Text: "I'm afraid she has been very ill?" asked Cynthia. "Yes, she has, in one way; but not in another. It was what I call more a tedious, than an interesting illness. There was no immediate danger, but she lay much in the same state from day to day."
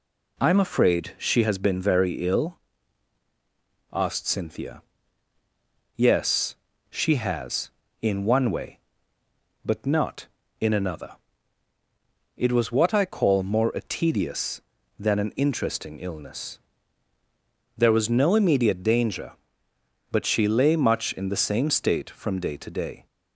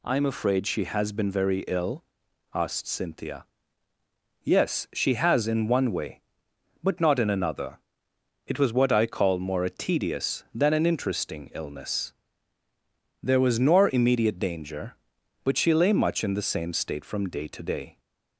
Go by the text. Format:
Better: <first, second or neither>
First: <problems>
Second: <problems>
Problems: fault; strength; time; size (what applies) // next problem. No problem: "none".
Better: first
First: none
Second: says "nor" for "no"; at 13.5 s